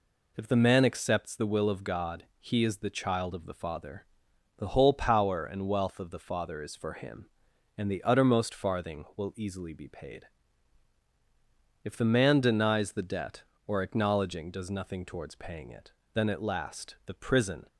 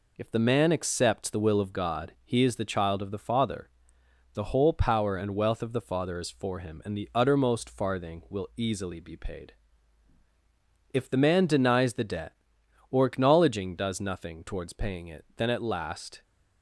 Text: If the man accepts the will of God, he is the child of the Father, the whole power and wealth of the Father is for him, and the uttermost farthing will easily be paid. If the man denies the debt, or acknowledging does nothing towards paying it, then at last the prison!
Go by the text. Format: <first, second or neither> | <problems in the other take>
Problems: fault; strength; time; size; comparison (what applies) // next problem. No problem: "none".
first | stops before "the prison"; at 16.2 s